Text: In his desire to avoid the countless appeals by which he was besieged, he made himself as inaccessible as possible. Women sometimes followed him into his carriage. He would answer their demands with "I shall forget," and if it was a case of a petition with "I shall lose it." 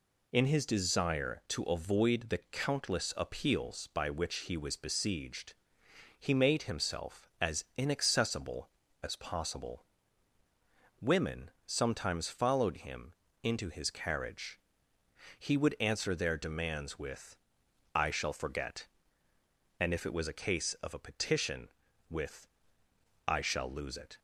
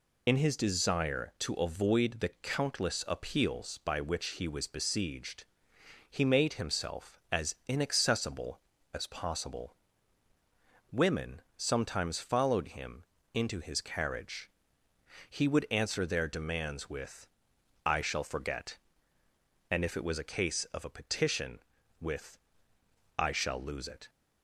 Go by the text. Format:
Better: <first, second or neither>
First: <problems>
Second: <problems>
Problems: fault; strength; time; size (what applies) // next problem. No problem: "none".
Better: first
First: pauses between "him" and "into"; slight; at 13.1 s; 0.30 s long // pauses between "with" and "I"; noticeable; at 17.3 s; 0.58 s long // pauses between "with" and "I"; noticeable; at 22.4 s; 0.80 s long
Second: loses the start of "In"; at 0.2 s; 40 ms // pauses between "him" and "into"; slight; at 13.0 s; 0.30 s long // pauses between "with" and "I"; noticeable; at 17.2 s; 0.58 s long // pauses between "with" and "I"; noticeable; at 22.3 s; 0.80 s long